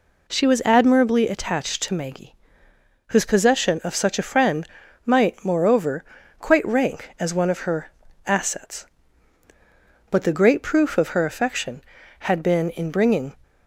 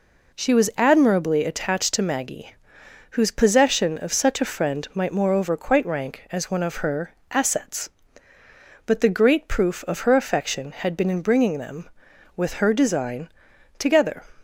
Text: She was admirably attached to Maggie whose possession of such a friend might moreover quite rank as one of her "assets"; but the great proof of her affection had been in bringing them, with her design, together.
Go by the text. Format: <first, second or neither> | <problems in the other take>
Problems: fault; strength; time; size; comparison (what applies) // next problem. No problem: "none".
second | pauses between "Maggie" and "whose"; noticeable; at 2.3 s; 0.76 s long; noticeable in the second // pauses between "friend" and "might"; at 4.6 s; 0.38 s long // pauses between "moreover" and "quite"; slight; at 6.0 s; 0.36 s long // pauses between "her" and "assets"; slight; at 7.9 s; 0.34 s long; slight in the second // stops before "them with her design together"; at 13.4 s